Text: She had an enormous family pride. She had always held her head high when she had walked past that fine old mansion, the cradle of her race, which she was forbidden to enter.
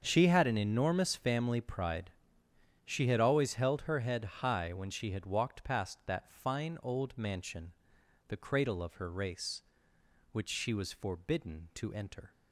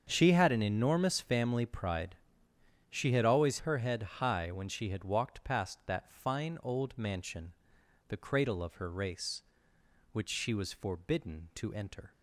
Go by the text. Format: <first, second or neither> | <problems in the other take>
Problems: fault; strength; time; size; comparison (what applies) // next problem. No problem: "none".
first | starts louder than the rest; until 1.1 s; 7 dB; also in the first // skips "held"; at 3.5 s // pauses between "head" and "high"; slight; at 4.0 s; 0.18 s long; slight in the first